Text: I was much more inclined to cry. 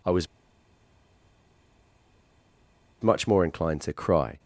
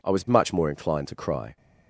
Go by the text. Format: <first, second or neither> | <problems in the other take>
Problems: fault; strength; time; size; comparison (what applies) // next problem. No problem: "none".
second | pauses between "was" and "much"; strong; at 0.2 s; 2.7 s long